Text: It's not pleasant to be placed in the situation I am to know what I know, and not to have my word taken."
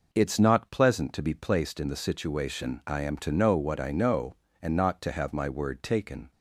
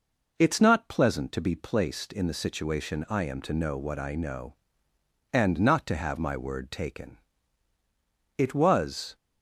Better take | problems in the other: first | goes on to say "It was"; noticeable; from 8.3 s on; 0.76 s long

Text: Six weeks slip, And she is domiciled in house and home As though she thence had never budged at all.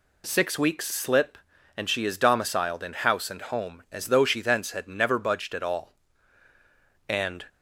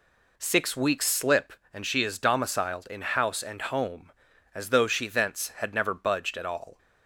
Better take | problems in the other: second | goes on to say "And"; slight; from 7.0 s on; 0.38 s long

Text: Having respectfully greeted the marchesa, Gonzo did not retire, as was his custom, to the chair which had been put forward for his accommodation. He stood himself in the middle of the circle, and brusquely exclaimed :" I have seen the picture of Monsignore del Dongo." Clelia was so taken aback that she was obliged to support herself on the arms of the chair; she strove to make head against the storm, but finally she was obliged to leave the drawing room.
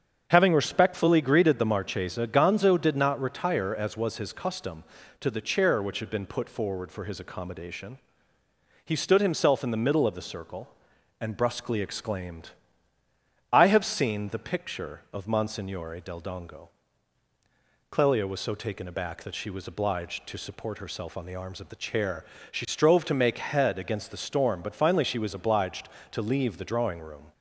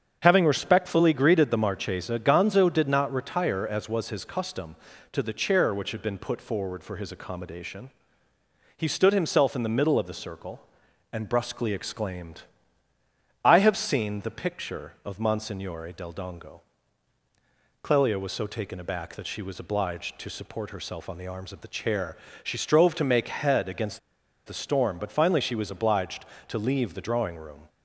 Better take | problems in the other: first | starts louder than the rest; strong; until 1.2 s; 7.5 dB; strong in the first // pauses between "against" and "the"; noticeable; at 23.9 s; 0.48 s long

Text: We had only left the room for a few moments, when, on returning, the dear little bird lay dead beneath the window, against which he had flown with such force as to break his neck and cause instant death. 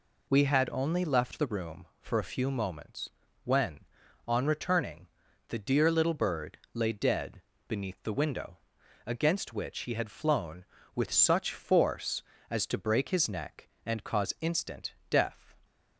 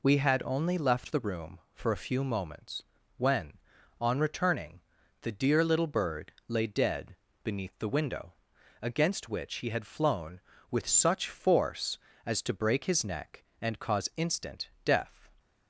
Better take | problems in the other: neither | pauses between "bird" and "lay"; slight; the same in both // pauses between "dead" and "beneath"; slight; the same in both // pauses between "instant" and "death"; slight; the same in both

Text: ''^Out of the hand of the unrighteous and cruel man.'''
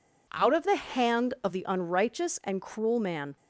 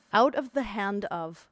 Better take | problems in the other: first | stops before "the unrighteous and cruel man"; at 1.4 s

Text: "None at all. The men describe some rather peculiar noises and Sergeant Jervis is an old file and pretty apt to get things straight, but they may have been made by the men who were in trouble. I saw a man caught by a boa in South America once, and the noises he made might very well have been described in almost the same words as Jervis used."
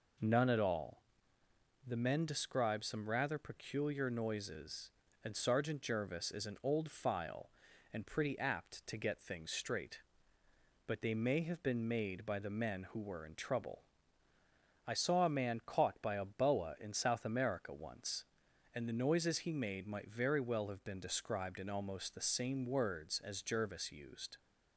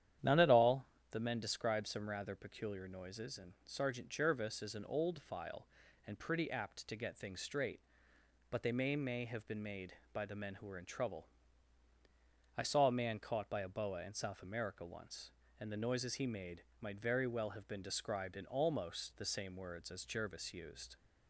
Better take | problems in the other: first | starts louder than the rest; strong; until 1.4 s; 10 dB // says "may" twice; at 8.9 s // pauses between "made" and "might"; slight; at 16.6 s; 0.18 s long

